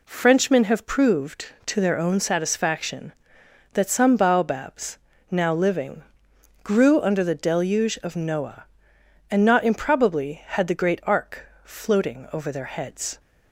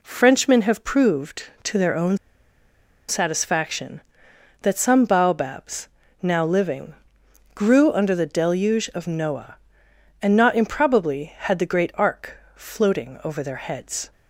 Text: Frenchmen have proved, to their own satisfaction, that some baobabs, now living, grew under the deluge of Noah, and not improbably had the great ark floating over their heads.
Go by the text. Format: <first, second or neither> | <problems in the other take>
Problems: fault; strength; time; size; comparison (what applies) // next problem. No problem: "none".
first | pauses between "own" and "satisfaction"; noticeable; at 2.1 s; 0.91 s long // pauses between "ark" and "floating"; slight; at 12.3 s; 0.18 s long; slight in the first